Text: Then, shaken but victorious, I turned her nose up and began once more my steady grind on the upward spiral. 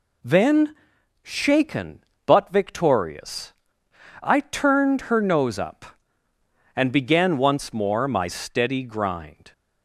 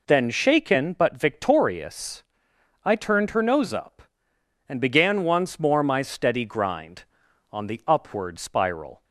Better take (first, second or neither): second